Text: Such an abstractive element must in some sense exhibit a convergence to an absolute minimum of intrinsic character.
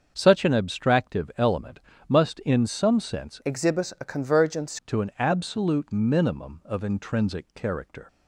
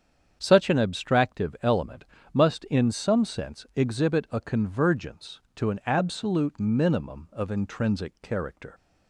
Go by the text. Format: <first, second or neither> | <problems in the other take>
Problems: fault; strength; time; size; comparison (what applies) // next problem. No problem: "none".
second | starts louder than the rest; until 1.1 s; 6.5 dB; strong in the second // pauses between "element" and "must"; slight; at 1.8 s; 0.28 s long; slight in the second // changes voice from "exhibit" to "convergence"; from 3.4 to 4.7 s; 1.3 s long